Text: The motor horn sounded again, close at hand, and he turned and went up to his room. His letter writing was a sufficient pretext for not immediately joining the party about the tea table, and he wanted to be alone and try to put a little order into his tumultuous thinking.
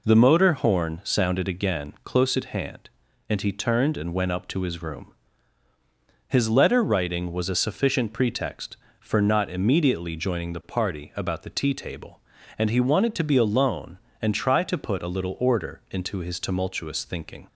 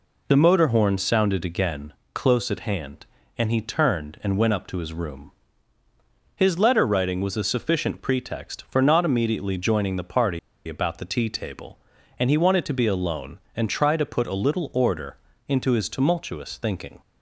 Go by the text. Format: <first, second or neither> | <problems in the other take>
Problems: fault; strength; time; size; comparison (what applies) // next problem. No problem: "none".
first | pauses between "party" and "about"; slight; at 10.3 s; 0.27 s long // pauses between "order" and "into"; slight; at 15.1 s; 0.30 s long